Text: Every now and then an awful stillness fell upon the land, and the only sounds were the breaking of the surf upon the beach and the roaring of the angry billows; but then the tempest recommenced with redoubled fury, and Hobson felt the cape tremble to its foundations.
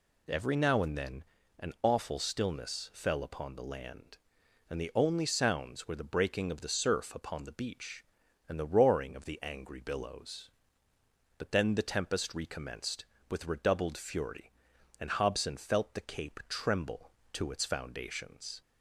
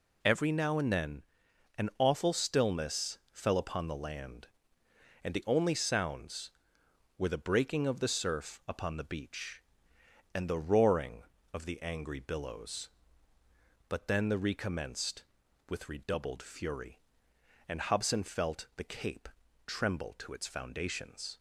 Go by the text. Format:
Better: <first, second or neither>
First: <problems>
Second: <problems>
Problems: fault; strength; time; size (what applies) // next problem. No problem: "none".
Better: first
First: pauses between "then" and "an"; slight; at 1.2 s; 0.34 s long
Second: pauses between "then" and "an"; noticeable; at 1.2 s; 0.56 s long // pauses between "stillness" and "fell"; slight; at 3.1 s; 0.16 s long // skips "tempest"; at 14.3 s // pauses between "cape" and "tremble"; at 19.2 s; 0.38 s long